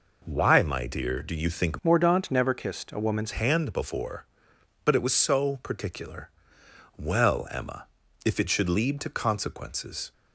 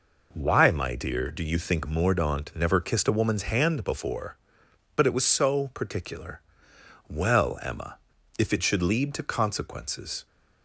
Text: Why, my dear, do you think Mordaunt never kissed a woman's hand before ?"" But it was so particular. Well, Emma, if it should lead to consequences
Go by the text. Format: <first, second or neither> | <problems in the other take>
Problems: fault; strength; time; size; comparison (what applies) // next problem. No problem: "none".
second | changes voice from "Mordaunt" to "woman's"; from 1.8 to 3.3 s; 1.5 s long